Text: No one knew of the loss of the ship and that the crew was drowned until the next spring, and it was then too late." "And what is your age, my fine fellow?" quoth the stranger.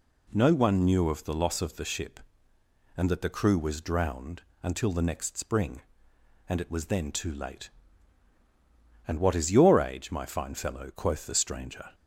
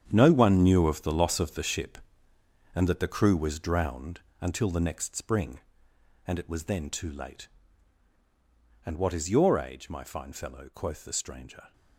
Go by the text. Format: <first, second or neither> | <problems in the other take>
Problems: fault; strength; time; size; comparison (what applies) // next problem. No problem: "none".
first | gets quieter; strong; throughout; 13 dB // pauses between "drowned" and "until"; slight; at 4.2 s; 0.20 s long; slight in the first